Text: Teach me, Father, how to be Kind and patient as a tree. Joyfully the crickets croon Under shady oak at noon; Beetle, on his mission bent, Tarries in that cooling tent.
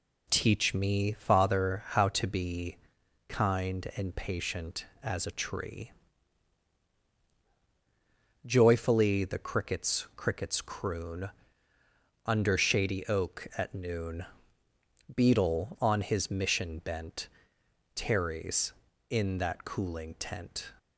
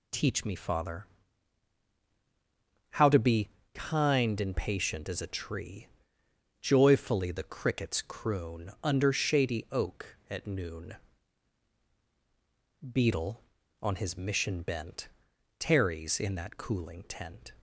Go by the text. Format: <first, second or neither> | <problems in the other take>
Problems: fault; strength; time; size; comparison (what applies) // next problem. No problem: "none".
second | pauses between "be" and "Kind"; noticeable; at 2.7 s; 0.52 s long; slight in the second // says "crickets" twice; at 10.1 s // pauses between "croon" and "Under"; noticeable; at 11.2 s; 0.96 s long